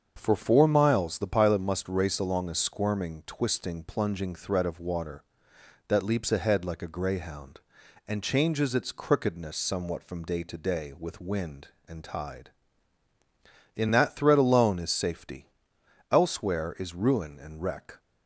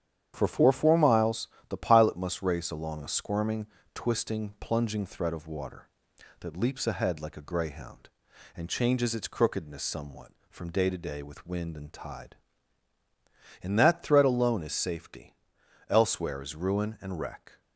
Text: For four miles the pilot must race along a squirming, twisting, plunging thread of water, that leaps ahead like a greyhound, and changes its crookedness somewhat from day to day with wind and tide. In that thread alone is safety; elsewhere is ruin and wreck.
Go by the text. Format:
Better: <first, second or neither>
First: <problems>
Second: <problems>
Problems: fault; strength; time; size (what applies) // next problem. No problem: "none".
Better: first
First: starts louder than the rest; until 1.1 s; 7 dB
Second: starts louder than the rest; strong; until 1.3 s; 9.5 dB // says "four" twice; at 0.7 s // pauses between "miles" and "the"; slight; at 1.4 s; 0.22 s long